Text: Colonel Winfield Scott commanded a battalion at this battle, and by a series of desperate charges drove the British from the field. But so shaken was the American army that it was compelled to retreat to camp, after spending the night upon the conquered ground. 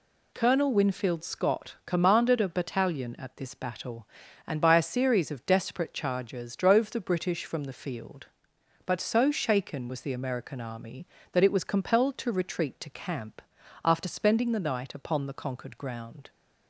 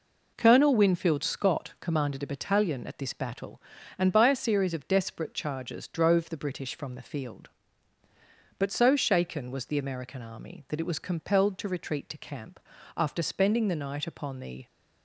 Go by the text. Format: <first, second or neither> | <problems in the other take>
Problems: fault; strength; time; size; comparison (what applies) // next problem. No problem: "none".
first | stops before "conquered ground"; at 14.6 s